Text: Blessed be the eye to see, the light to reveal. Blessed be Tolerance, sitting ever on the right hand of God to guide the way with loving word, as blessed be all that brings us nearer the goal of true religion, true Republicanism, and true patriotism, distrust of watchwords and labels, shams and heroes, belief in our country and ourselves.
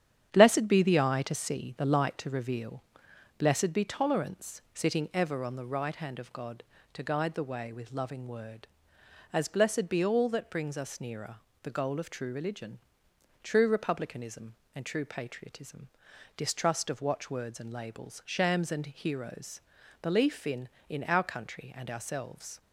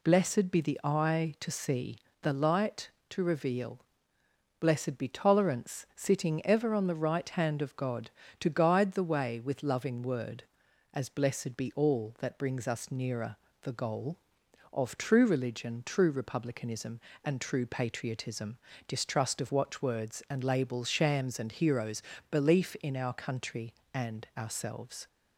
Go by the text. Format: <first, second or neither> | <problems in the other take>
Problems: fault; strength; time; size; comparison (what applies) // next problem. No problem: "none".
second | starts louder than the rest; strong; until 1.3 s; 9.5 dB // pauses between "nearer" and "the"; slight; at 11.3 s; 0.28 s long; slight in the second // says "in" twice; at 20.8 s